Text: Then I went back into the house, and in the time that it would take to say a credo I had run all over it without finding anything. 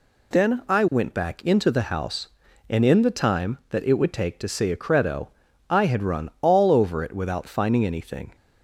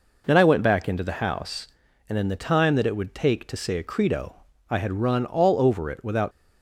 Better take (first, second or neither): first